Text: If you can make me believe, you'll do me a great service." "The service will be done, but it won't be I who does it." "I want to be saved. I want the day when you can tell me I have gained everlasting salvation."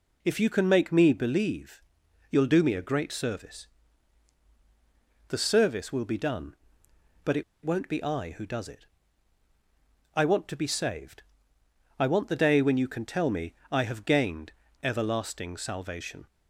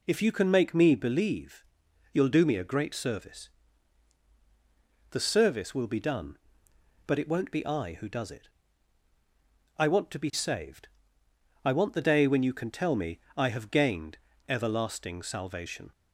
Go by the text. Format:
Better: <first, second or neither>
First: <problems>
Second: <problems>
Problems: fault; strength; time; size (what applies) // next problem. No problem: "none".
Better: second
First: pauses between "it" and "won't"; slight; at 7.4 s; 0.22 s long // pauses between "me" and "I"; slight; at 13.5 s; 0.16 s long // pauses between "gained" and "everlasting"; slight; at 14.5 s; 0.28 s long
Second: pauses between "me" and "I"; slight; at 13.1 s; 0.16 s long // pauses between "gained" and "everlasting"; slight; at 14.1 s; 0.28 s long